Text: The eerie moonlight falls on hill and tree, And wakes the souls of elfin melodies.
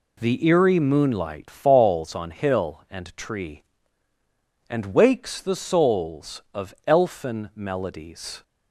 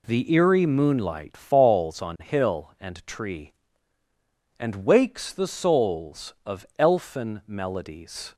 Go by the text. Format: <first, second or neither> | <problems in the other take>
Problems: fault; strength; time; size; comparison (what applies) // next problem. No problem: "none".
neither | none